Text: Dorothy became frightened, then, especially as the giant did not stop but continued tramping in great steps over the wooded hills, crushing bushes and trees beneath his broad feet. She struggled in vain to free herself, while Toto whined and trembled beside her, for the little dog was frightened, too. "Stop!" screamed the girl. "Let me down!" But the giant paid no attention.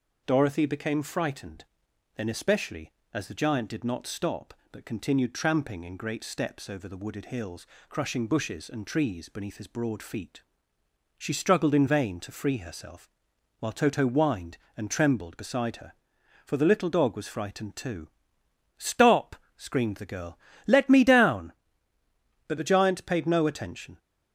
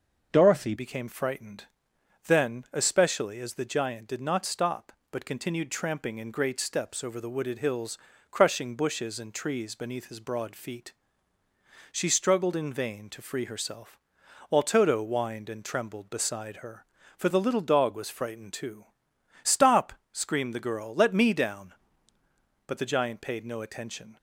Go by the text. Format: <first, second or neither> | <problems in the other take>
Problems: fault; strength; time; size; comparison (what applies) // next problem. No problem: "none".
first | changes voice at "became"; from 0.7 s on; 23.4 s long